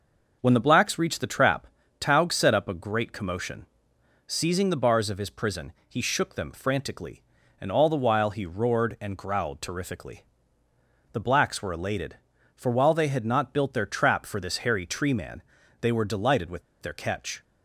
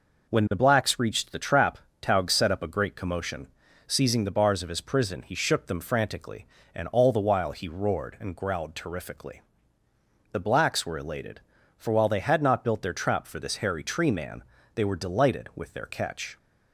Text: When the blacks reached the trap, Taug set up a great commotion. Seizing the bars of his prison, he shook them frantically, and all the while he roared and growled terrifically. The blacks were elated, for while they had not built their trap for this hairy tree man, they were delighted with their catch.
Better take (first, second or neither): second